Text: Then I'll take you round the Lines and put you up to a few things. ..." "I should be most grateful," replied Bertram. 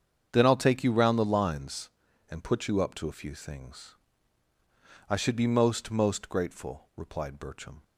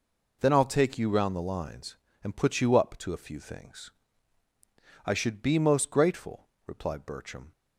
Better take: second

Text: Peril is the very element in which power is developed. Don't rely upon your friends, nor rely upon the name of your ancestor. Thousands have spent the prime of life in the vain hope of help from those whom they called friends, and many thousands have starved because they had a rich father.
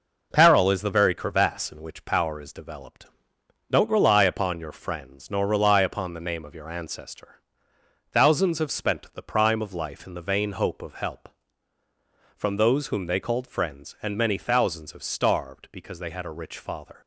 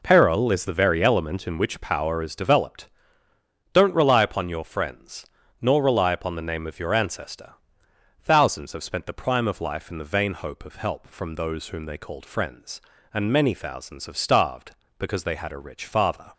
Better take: second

